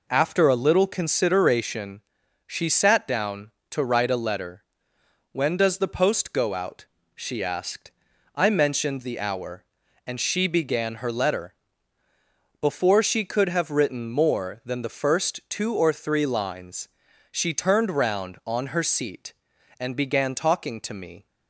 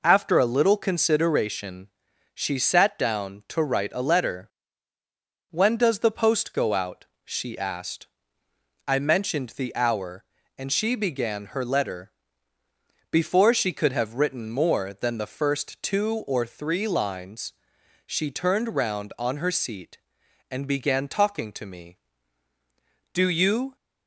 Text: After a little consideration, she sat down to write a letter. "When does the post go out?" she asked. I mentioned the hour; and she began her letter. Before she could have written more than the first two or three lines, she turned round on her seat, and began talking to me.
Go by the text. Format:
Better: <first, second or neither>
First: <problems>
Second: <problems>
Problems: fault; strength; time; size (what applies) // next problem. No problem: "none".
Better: first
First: none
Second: goes on to say "Do you"; noticeable; from 23.1 s on; 0.62 s long